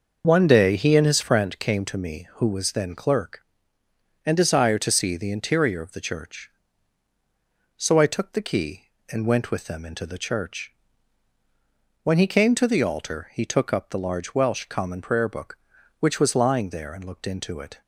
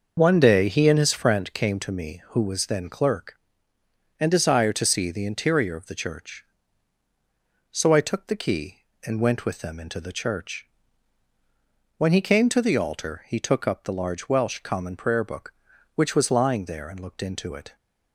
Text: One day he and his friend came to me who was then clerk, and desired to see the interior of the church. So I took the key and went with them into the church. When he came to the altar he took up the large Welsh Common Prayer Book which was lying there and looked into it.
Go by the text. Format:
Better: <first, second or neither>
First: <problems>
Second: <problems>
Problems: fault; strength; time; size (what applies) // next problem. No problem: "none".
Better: neither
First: starts louder than the rest; noticeable; until 1.2 s; 6 dB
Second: starts louder than the rest; noticeable; until 1.1 s; 6 dB